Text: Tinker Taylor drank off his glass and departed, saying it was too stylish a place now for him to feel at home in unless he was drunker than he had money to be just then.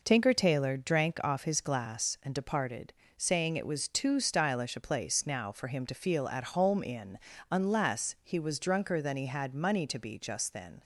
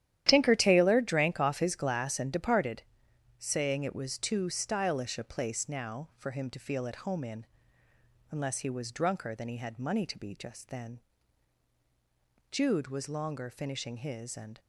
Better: first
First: pauses between "in" and "unless"; slight; at 7.1 s; 0.32 s long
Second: starts louder than the rest; strong; until 1.2 s; 11.5 dB // pauses between "in" and "unless"; noticeable; at 7.4 s; 0.84 s long // goes on to say "Jude was longer finishing his and"; strong; from 12.5 s on; 2.0 s long

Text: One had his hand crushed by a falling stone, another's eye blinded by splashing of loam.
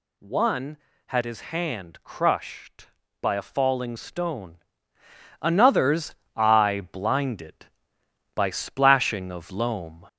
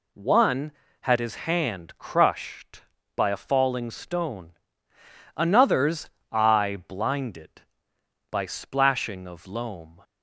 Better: second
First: gets louder; throughout; 3.5 dB // pauses between "another's" and "eye"; slight; at 6.1 s; 0.21 s long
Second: pauses between "another's" and "eye"; slight; at 6.0 s; 0.22 s long

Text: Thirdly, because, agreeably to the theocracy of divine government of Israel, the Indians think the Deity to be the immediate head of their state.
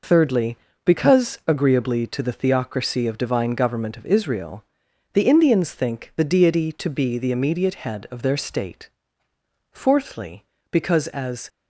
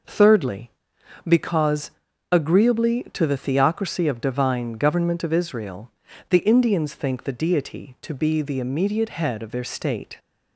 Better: second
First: goes on to say "Fourthly because as"; strong; from 9.7 s on; 1.7 s long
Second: none

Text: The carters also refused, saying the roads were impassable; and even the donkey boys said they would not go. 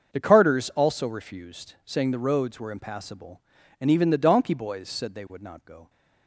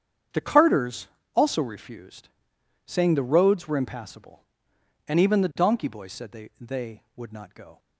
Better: first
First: starts louder than the rest; until 1.1 s; 6.5 dB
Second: starts louder than the rest; strong; until 1.6 s; 8 dB // pauses between "carters" and "also"; slight; at 1.0 s; 0.28 s long // says "they" twice; at 6.5 s

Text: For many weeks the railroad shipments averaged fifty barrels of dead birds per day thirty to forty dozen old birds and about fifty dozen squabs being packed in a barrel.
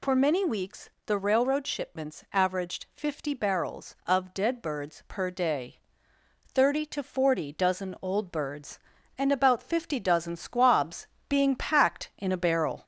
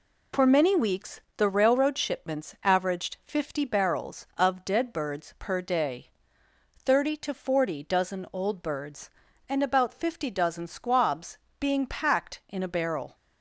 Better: second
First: gets louder; slight; throughout; 2.5 dB // pauses between "weeks" and "the"; slight; at 0.8 s; 0.16 s long // pauses between "day" and "thirty"; noticeable; at 5.7 s; 0.68 s long // pauses between "squabs" and "being"; slight; at 11.0 s; 0.24 s long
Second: pauses between "weeks" and "the"; slight; at 1.2 s; 0.16 s long // pauses between "day" and "thirty"; noticeable; at 6.0 s; 0.68 s long // pauses between "squabs" and "being"; slight; at 11.3 s; 0.24 s long

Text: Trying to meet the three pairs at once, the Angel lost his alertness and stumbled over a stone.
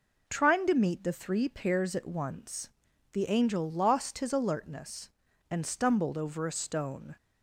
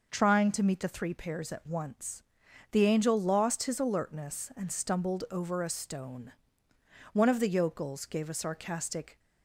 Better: first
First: none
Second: goes on to say "One of the yokels gave a sarcastic"; strong; from 7.1 s on; 2.0 s long

